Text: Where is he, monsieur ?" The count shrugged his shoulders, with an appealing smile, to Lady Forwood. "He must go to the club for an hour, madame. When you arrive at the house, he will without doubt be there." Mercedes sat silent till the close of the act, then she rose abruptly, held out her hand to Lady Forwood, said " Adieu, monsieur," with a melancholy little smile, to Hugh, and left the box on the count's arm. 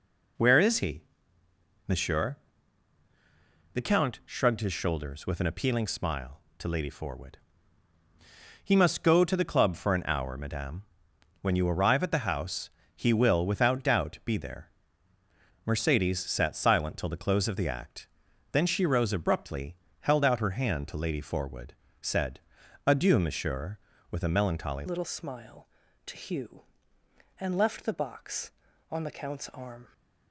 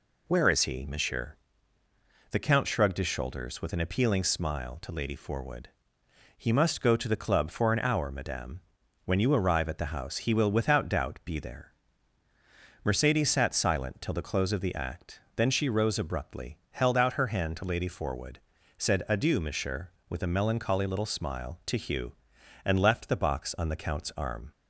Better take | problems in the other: second | changes voice at "little"; from 24.8 s on; 5.1 s long

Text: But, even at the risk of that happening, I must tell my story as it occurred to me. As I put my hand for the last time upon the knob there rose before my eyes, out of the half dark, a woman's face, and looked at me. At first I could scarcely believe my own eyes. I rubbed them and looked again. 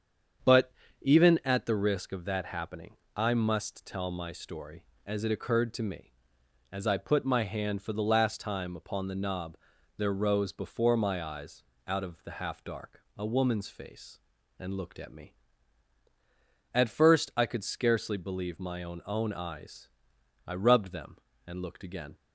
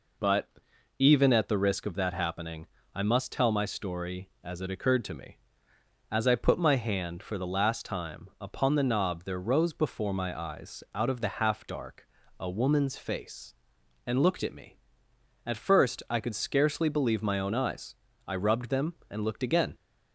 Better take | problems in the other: second | starts louder than the rest; strong; until 1.7 s; 7.5 dB // pauses between "knob" and "there"; at 9.5 s; 0.40 s long // says "own" twice; at 19.0 s

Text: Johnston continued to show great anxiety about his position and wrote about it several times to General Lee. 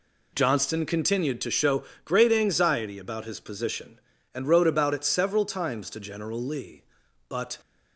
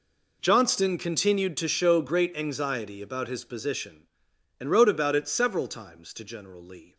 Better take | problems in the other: second | pauses between "show" and "great"; slight; at 1.8 s; 0.20 s long // goes on to say "But"; slight; from 7.2 s on; 0.30 s long

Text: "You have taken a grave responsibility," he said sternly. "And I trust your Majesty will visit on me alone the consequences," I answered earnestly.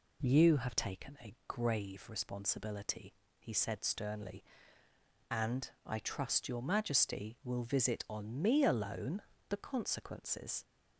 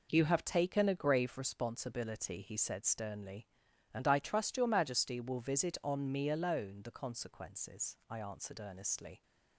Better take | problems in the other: second | pauses between "alone" and "the"; slight; at 9.2 s; 0.26 s long // stops before "I answered earnestly"; at 10.6 s

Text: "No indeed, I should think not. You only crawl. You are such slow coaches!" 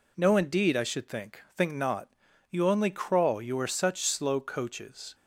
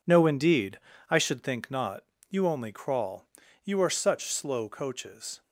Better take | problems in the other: second | says "think" twice; at 1.5 s

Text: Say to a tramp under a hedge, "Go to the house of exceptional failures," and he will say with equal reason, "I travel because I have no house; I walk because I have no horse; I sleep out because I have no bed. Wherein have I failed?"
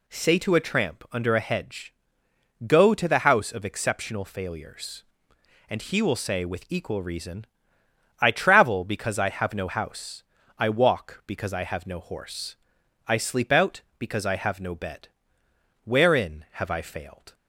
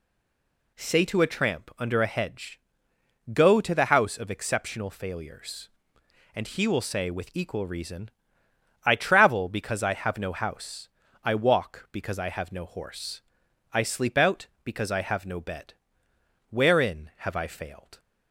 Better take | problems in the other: first | stays silent before the first word; slight; until 0.7 s; 0.7 s long

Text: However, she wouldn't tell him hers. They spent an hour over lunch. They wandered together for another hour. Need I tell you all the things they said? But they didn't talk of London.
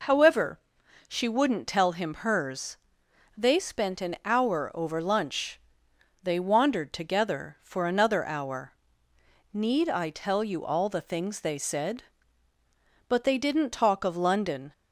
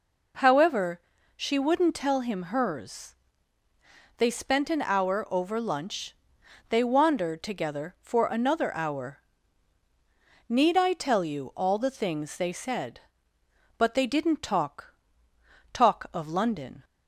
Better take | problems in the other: first | says "talk" twice; at 15.7 s

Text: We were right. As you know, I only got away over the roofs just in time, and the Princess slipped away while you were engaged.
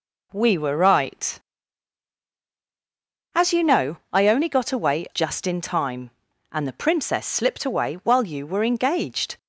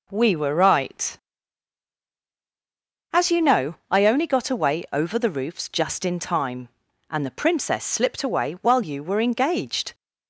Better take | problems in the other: second | skips "over the roofs"; at 5.0 s

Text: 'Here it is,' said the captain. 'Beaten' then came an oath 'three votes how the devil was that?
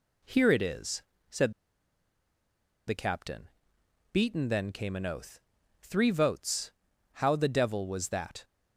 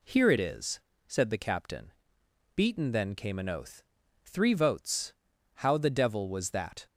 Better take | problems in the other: second | pauses between "said" and "the"; strong; at 1.5 s; 1.3 s long // pauses between "oath" and "three"; at 5.3 s; 0.42 s long; also in the second // pauses between "votes" and "how"; at 6.6 s; 0.44 s long; also in the second

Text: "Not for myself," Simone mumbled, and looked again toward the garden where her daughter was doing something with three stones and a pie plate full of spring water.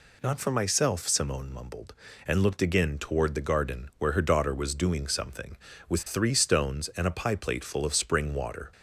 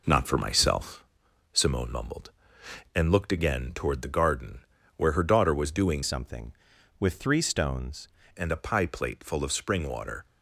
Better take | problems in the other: first | pauses between "garden" and "where"; slight; at 4.6 s; 0.32 s long // changes voice from "something" to "stones"; from 6.0 to 8.0 s; 2.0 s long

